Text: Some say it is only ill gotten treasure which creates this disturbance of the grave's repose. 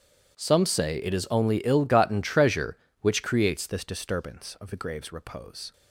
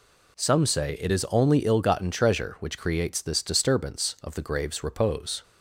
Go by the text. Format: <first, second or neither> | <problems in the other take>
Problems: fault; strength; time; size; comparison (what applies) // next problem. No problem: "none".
second | starts louder than the rest; strong; until 1.3 s; 10 dB // changes voice at "this"; from 3.6 s on; 2.1 s long